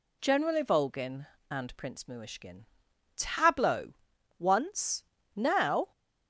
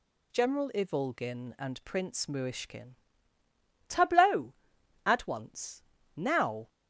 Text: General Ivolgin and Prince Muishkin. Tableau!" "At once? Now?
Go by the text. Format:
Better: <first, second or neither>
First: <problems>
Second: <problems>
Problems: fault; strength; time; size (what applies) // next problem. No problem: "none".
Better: second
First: skips "At"; at 4.1 s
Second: none